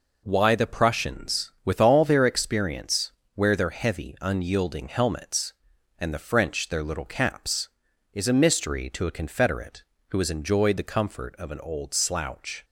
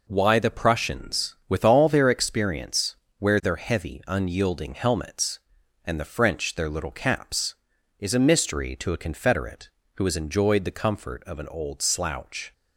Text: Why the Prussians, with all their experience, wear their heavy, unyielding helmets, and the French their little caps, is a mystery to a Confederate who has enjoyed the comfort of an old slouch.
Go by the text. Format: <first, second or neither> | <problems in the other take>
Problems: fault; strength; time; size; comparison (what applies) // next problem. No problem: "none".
neither | none